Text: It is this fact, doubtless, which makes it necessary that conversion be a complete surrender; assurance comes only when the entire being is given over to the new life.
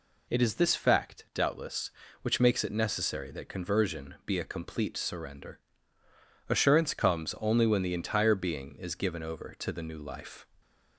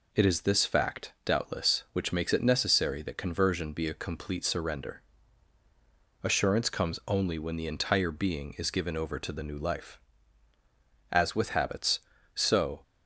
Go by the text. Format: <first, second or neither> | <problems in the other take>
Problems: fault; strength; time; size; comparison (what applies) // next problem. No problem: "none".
first | goes on to say "As with habits so"; strong; from 11.1 s on; 1.6 s long